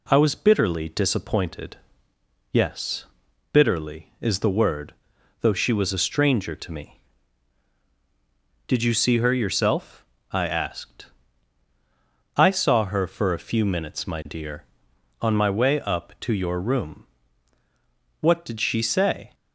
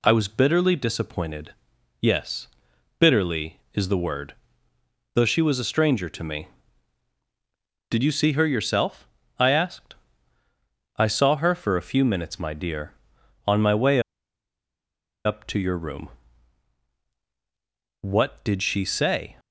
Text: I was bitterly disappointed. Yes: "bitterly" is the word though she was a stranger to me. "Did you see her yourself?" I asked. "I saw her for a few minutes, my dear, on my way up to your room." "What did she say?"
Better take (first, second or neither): first